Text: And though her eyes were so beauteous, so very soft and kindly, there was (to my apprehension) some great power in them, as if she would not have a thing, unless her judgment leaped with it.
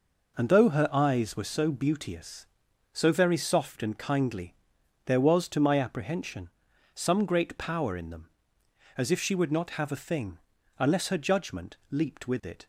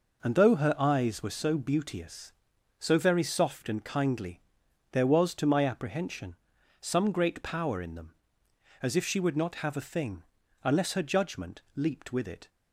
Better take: neither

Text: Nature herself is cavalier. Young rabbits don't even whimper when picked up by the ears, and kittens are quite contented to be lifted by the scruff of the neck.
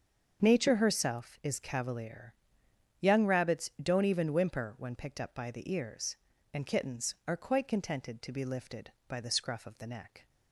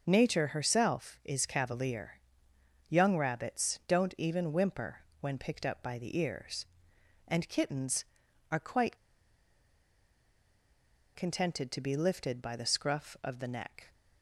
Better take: first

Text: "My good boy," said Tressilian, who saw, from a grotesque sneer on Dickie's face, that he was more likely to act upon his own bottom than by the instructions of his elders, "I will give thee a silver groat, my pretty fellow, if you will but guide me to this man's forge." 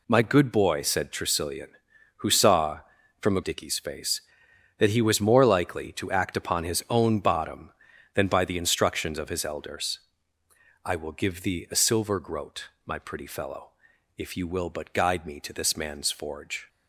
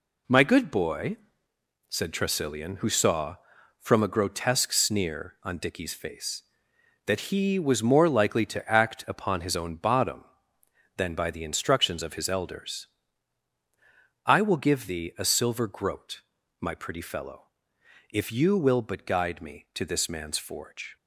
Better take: second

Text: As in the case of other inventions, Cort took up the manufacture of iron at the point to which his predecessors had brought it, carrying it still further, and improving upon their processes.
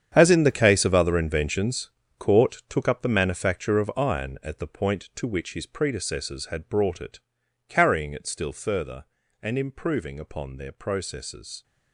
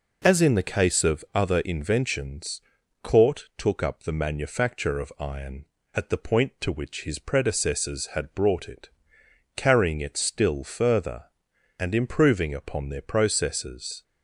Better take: second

